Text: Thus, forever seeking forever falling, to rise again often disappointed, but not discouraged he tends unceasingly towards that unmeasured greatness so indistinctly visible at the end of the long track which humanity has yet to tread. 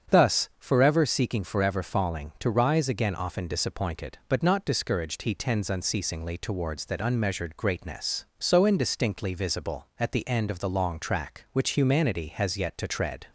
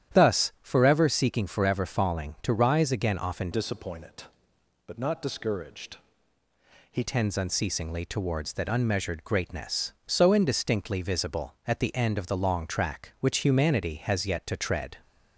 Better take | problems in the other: first | starts louder than the rest; strong; until 1.2 s; 10.5 dB; strong in the first // changes voice from "disappointed" to "he"; from 3.5 to 7.0 s; 3.5 s long // pauses between "discouraged" and "he"; noticeable; at 5.9 s; 0.94 s long

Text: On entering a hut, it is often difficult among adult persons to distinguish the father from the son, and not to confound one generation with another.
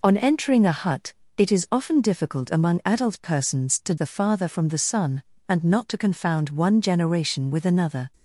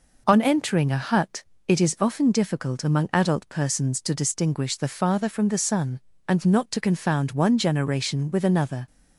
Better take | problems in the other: second | skips "distinguish"; at 3.9 s

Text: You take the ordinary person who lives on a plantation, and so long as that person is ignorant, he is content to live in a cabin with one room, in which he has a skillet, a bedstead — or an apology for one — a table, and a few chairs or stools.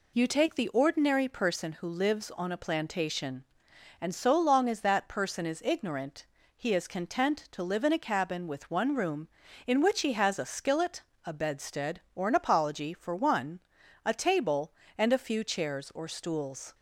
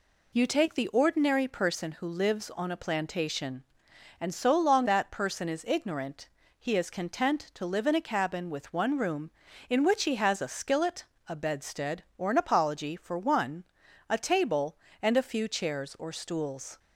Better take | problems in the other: first | skips "as"; at 4.8 s

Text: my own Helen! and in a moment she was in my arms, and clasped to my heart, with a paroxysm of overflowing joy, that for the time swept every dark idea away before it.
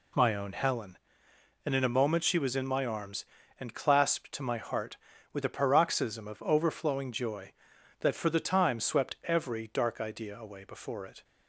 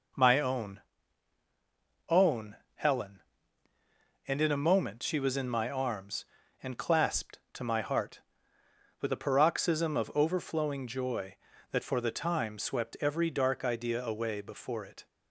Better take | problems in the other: first | says "own" twice; at 2.0 s

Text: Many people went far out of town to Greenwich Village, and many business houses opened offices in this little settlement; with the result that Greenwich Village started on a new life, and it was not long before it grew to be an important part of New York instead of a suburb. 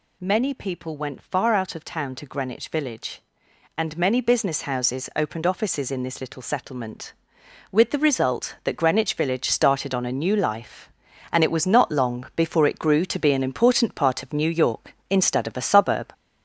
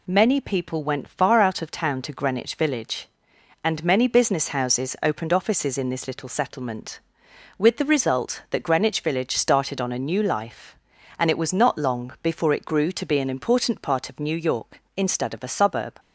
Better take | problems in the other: second | gets louder; noticeable; throughout; 4.5 dB

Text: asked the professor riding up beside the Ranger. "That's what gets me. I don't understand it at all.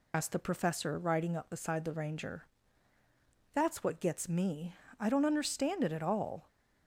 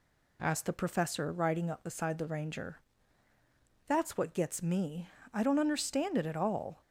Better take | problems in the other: second | loses the start of "asked"; at 0.1 s; 85 ms

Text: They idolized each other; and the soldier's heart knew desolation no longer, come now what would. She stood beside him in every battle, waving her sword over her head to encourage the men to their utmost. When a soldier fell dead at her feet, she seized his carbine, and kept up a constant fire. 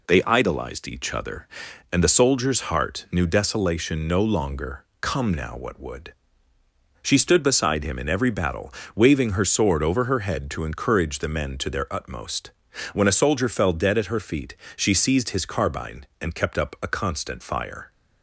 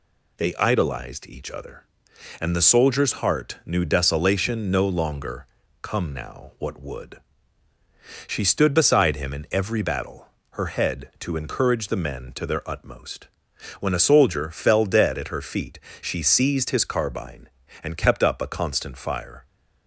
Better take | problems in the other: first | skips "waving her sword over"; at 10.3 s

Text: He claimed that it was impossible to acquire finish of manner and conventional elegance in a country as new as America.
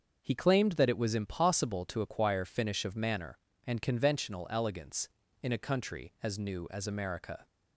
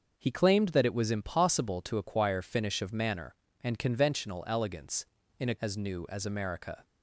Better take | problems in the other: first | starts louder than the rest; until 1.1 s; 6 dB; also in the first // skips "country"; at 5.5 s

